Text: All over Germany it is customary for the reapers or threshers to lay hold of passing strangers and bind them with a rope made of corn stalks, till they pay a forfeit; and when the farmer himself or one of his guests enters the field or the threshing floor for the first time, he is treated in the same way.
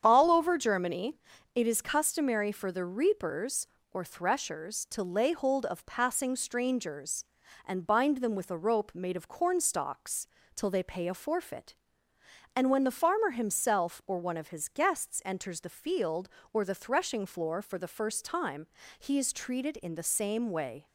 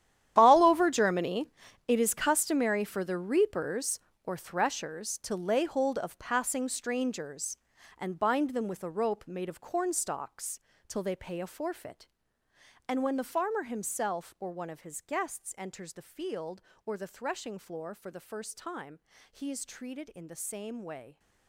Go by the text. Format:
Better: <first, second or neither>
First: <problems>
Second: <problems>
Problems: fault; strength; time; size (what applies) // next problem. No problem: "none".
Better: first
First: starts louder than the rest; strong; until 1.0 s; 8 dB // pauses between "Germany" and "it"; slight; at 1.1 s; 0.36 s long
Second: gets quieter; strong; throughout; 16.5 dB // starts louder than the rest; strong; until 1.3 s; 11 dB // pauses between "Germany" and "it"; slight; at 1.5 s; 0.36 s long